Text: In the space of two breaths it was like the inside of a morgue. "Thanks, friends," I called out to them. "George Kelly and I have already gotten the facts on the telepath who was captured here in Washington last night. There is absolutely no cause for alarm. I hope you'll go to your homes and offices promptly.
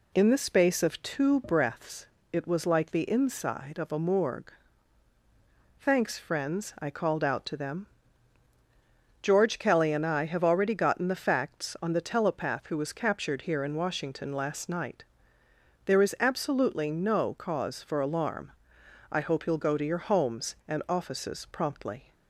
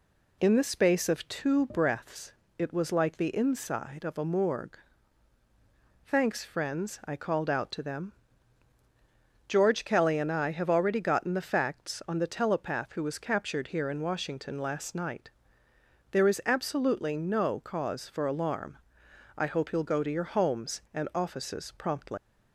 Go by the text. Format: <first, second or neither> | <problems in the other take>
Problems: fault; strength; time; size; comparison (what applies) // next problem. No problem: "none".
first | pauses between "breaths" and "it"; slight; at 2.3 s; 0.26 s long; slight in the first // leaves "promptly" unfinished; at 22.1 s; 205 ms